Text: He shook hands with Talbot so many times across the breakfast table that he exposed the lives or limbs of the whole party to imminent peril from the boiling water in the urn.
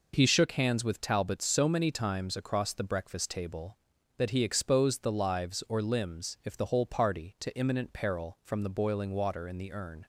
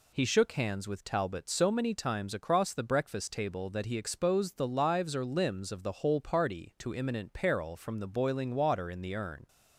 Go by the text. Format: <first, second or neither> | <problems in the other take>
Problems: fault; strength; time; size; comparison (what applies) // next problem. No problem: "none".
second | says "if" for "of"; at 6.4 s